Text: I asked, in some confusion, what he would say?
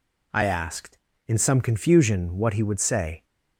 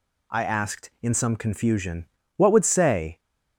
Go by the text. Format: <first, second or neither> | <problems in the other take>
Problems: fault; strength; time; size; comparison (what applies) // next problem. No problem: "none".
first | skips "he"; at 2.5 s